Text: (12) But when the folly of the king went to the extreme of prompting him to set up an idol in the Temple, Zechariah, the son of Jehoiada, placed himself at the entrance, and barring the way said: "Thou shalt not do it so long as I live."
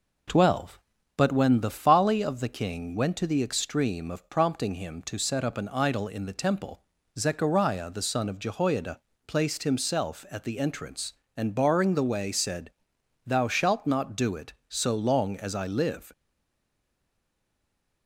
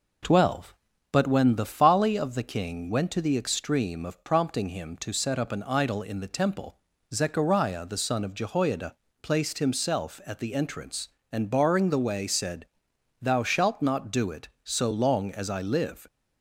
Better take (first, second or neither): second